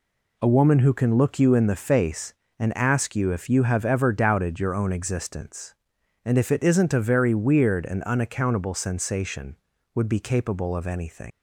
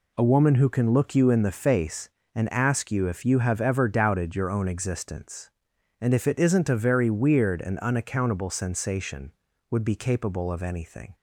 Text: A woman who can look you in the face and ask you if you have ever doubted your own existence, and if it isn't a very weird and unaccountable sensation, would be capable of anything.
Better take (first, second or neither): second